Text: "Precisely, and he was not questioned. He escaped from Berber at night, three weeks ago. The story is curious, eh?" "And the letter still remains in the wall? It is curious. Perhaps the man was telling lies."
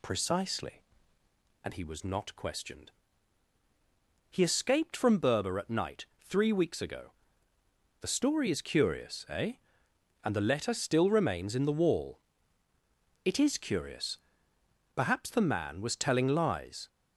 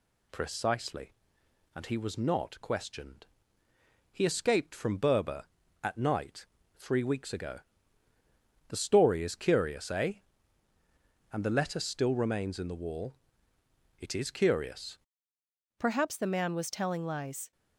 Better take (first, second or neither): first